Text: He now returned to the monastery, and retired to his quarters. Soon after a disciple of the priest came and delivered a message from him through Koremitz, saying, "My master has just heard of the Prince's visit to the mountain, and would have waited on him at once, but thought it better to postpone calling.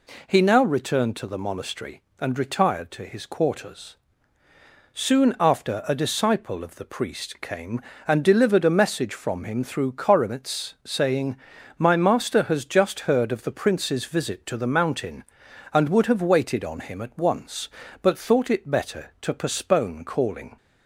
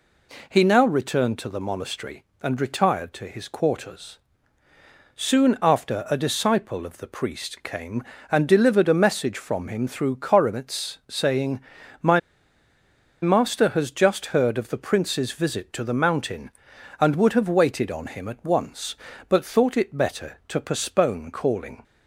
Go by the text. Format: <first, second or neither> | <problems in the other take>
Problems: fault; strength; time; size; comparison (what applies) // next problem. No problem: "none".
first | pauses between "My" and "master"; at 12.1 s; 1.0 s long